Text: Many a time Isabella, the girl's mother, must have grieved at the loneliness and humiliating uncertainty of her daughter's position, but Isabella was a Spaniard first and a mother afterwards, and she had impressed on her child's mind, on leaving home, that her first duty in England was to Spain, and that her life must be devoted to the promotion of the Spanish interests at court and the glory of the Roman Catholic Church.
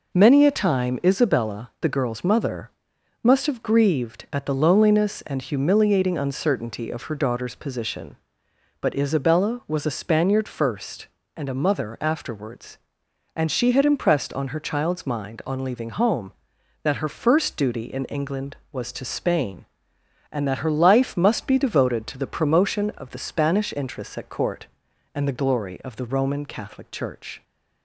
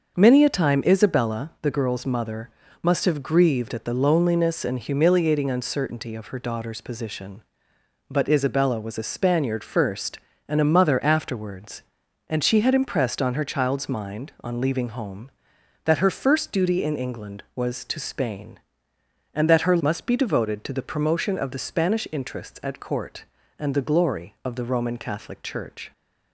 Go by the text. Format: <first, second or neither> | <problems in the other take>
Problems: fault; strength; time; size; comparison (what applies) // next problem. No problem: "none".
first | starts louder than the rest; until 1.1 s; 6 dB // skips "life"; at 19.8 s